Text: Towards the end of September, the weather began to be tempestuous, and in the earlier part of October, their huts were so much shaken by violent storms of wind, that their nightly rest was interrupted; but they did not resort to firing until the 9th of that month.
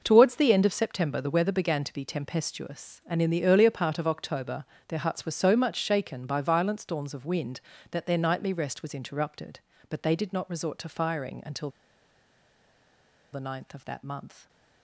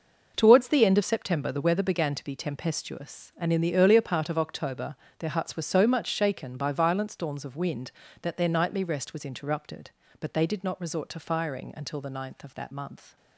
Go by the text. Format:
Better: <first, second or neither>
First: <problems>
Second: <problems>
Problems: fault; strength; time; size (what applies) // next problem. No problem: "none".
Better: second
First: pauses between "until" and "the"; strong; at 11.7 s; 1.6 s long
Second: none